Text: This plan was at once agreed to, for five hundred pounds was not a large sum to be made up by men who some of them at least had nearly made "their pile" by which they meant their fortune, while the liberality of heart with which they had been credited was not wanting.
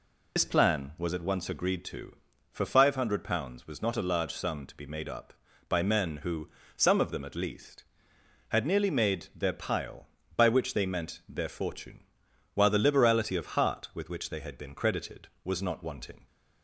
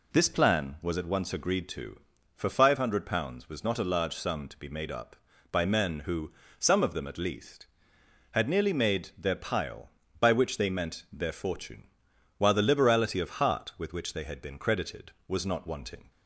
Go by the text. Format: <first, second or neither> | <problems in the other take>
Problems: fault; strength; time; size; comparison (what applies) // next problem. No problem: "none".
second | loses the start of "This"; at 0.3 s; 80 ms // pauses between "who" and "some"; slight; at 6.4 s; 0.26 s long; slight in the second